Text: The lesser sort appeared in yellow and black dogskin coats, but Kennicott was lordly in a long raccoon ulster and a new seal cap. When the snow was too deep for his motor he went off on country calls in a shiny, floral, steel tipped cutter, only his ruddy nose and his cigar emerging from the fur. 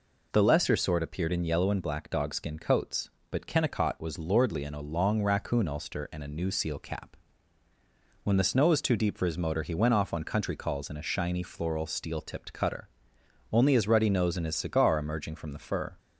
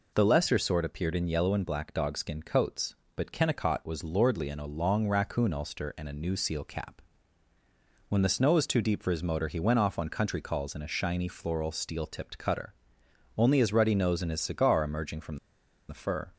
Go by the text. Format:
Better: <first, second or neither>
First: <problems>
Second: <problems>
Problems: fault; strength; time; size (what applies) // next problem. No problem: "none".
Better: first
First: none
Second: pauses between "from" and "the"; noticeable; at 15.3 s; 0.52 s long